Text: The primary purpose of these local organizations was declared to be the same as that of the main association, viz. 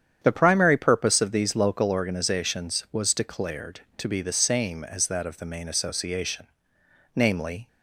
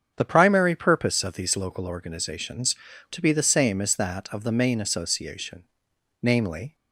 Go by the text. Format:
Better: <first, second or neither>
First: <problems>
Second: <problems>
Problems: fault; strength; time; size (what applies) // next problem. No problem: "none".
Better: first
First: starts louder than the rest; strong; until 1.2 s; 8.5 dB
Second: starts louder than the rest; strong; until 1.1 s; 7.5 dB // skips "was declared"; at 2.9 s